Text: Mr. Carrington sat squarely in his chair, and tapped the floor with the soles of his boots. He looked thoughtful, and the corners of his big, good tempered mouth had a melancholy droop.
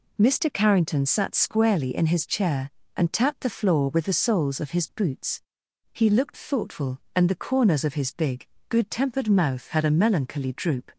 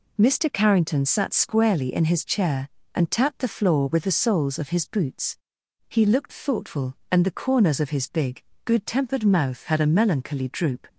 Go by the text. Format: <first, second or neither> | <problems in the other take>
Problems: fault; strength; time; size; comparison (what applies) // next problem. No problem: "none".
neither | none